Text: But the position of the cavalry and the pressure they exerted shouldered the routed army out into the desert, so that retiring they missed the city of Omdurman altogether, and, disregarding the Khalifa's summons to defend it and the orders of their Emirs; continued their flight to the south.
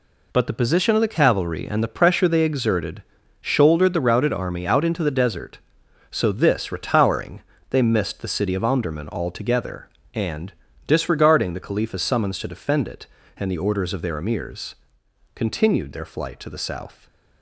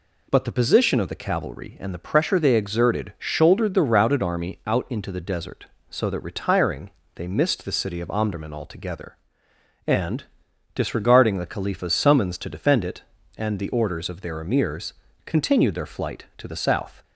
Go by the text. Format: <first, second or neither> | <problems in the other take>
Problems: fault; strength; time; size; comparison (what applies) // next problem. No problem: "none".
second | pauses between "exerted" and "shouldered"; at 3.0 s; 0.38 s long // says "this" for "that"; at 6.3 s // pauses between "retiring" and "they"; slight; at 7.4 s; 0.30 s long; slight in the second